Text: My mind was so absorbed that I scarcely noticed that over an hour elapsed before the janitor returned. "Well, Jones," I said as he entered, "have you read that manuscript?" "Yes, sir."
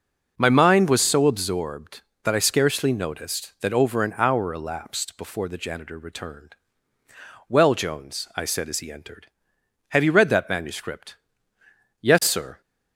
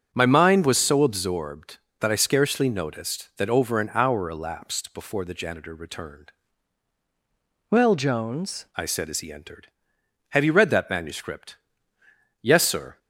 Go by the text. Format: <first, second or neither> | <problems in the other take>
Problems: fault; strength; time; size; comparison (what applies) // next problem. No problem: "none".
first | starts louder than the rest; strong; until 1.1 s; 7.5 dB // changes voice from "Well" to "Jones"; from 7.6 to 8.6 s; 1.0 s long